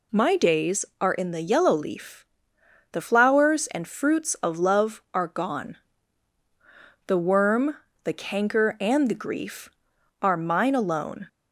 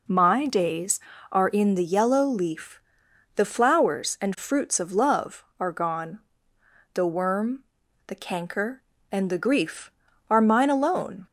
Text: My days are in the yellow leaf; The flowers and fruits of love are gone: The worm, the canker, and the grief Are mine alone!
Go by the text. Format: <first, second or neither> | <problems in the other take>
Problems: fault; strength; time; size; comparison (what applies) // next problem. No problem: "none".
neither | none